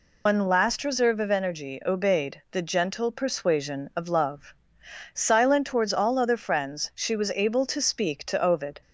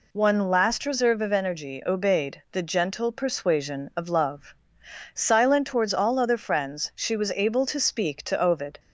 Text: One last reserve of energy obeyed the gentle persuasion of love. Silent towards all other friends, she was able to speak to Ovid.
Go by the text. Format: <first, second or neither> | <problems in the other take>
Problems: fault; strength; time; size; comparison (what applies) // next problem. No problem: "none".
second | loses the start of "One"; at 0.2 s; 130 ms